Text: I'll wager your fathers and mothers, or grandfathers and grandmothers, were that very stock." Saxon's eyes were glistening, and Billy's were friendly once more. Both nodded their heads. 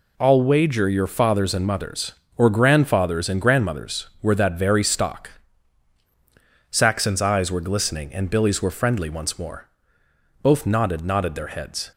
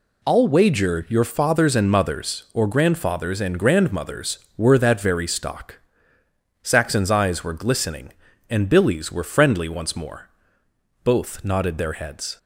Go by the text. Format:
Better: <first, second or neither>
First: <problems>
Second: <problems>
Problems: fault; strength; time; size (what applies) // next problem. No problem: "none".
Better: second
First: says "nodded" twice; at 11.0 s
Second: none